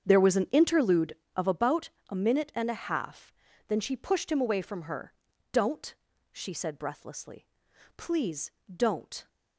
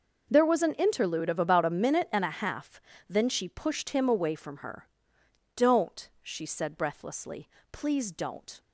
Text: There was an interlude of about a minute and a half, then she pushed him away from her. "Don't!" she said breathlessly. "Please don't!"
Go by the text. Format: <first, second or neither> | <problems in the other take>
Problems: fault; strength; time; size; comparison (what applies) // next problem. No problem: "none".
second | starts louder than the rest; strong; until 1.6 s; 7.5 dB // pauses between "about" and "a"; slight; at 1.8 s; 0.20 s long // pauses between "Please" and "don't"; slight; at 8.4 s; 0.26 s long